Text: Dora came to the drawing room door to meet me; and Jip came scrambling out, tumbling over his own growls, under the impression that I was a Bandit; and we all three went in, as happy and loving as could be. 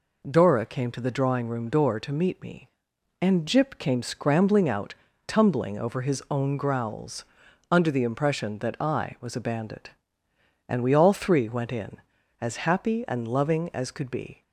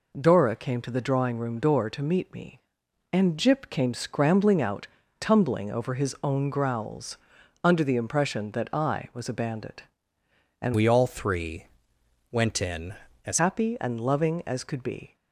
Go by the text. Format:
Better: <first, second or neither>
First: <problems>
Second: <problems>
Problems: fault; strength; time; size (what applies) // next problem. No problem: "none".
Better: first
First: none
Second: changes voice from "we" to "as"; from 10.7 to 13.3 s; 2.6 s long // pauses between "three" and "went"; noticeable; at 11.6 s; 0.66 s long